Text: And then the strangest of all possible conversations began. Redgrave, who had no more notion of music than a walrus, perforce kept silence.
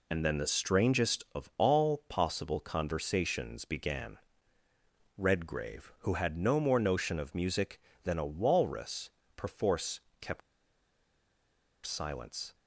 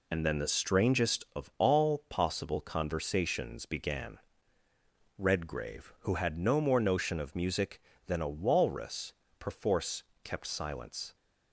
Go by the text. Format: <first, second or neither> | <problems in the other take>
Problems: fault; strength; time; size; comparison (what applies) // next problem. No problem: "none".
second | pauses between "perforce" and "kept"; slight; at 9.9 s; 0.20 s long; slight in the second // pauses between "kept" and "silence"; strong; at 10.4 s; 1.4 s long